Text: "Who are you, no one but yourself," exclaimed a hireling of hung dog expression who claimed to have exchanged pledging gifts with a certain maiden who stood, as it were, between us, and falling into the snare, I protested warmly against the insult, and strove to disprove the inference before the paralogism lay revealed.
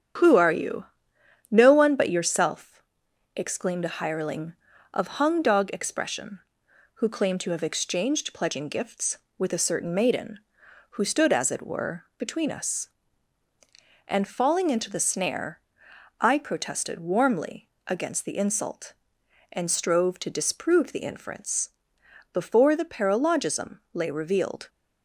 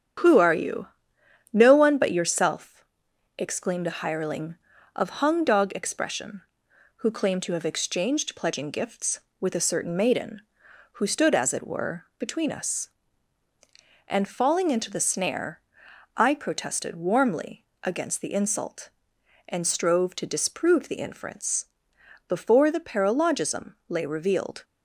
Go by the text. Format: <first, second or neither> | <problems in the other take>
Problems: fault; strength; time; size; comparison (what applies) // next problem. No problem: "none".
neither | starts louder than the rest; strong; the same in both // pauses between "warmly" and "against"; slight; the same in both // pauses between "inference" and "before"; noticeable; the same in both